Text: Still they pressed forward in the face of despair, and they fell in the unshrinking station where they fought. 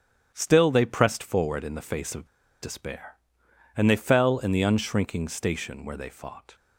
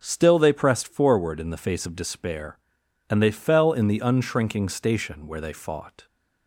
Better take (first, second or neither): second